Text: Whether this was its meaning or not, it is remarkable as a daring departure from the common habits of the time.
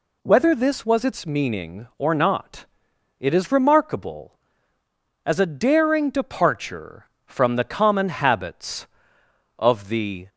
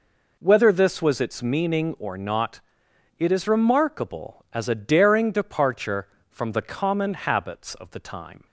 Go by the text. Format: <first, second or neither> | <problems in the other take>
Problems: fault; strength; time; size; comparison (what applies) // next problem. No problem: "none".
second | stops before "time"; at 10.2 s